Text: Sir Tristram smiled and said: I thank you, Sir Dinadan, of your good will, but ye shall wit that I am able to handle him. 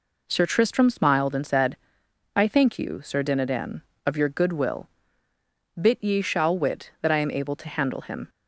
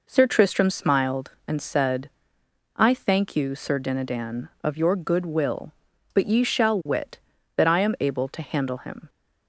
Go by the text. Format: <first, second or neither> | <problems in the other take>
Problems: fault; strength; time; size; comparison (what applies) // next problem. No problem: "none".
second | says "bit" for "but"; at 5.7 s